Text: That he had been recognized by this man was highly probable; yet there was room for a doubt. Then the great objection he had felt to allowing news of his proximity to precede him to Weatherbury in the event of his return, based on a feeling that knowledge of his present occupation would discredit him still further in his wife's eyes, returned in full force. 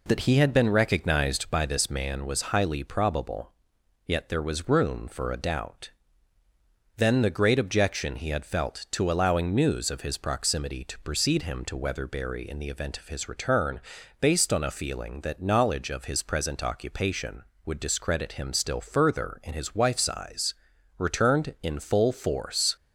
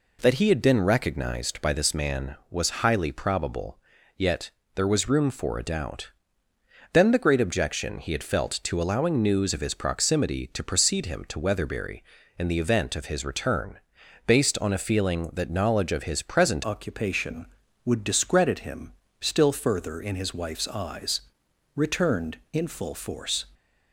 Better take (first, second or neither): first